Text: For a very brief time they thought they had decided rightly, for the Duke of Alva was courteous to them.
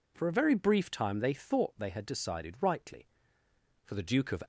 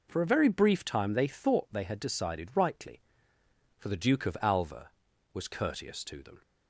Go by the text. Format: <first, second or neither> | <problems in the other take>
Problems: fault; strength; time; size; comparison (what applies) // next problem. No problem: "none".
second | stops before "Alva was courteous to them"; at 4.4 s